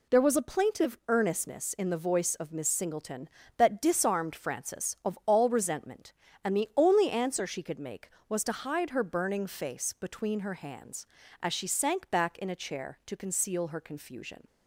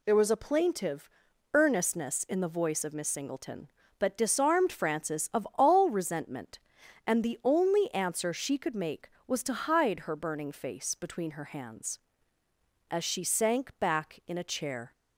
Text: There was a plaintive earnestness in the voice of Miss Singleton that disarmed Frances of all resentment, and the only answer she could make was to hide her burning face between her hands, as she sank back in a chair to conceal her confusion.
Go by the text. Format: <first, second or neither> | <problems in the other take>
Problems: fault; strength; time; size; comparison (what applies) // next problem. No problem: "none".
first | pauses between "plaintive" and "earnestness"; noticeable; at 1.0 s; 0.46 s long // stops before "to conceal her confusion"; at 14.9 s